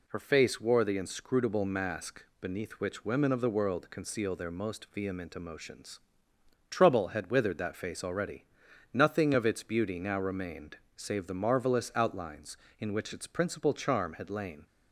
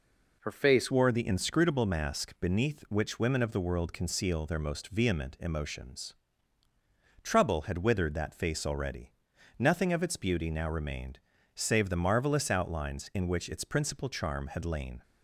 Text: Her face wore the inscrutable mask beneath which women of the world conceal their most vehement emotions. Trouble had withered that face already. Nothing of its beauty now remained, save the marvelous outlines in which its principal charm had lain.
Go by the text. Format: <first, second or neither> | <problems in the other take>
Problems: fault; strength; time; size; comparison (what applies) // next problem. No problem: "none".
first | changes voice at "wore"; from 0.9 s on; 14.1 s long